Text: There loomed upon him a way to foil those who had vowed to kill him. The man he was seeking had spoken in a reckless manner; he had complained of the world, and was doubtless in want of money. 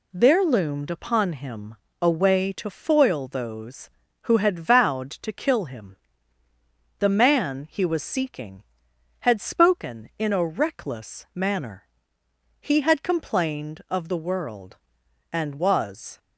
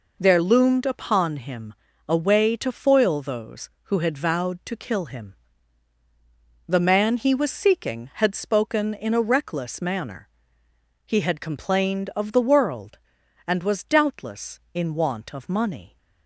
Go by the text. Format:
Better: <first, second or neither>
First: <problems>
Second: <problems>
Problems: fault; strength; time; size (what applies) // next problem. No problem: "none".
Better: second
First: pauses between "him" and "a"; slight; at 1.7 s; 0.26 s long // stops before "doubtless in want of money"; at 16.1 s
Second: pauses between "him" and "a"; slight; at 1.7 s; 0.34 s long